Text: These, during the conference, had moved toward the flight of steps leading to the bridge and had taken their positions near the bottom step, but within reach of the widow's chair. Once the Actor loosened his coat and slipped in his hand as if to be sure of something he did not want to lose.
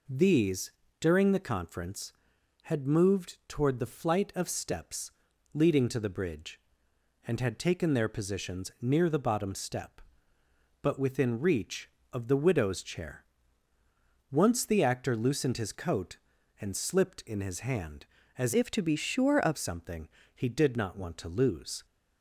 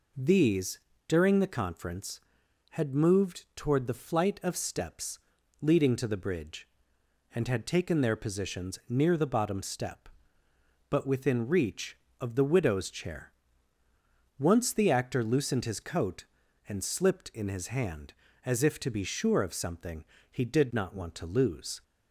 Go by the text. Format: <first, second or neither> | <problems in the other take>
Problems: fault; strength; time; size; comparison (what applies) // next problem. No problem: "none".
second | pauses between "steps" and "leading"; at 5.1 s; 0.42 s long; also in the second // changes voice from "if" to "of"; from 18.5 to 19.5 s; 1.0 s long // pauses between "something" and "he"; slight; at 20.0 s; 0.26 s long; slight in the second